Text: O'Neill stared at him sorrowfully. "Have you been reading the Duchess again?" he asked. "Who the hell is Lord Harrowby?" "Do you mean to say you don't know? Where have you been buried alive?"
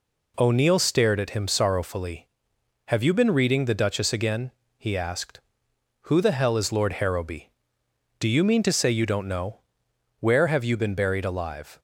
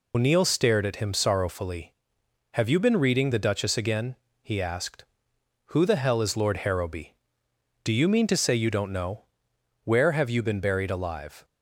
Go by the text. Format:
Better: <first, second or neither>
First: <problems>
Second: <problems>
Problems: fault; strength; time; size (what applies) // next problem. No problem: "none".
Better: first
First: none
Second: loses the start of "O'Neill"; at 0.1 s; 125 ms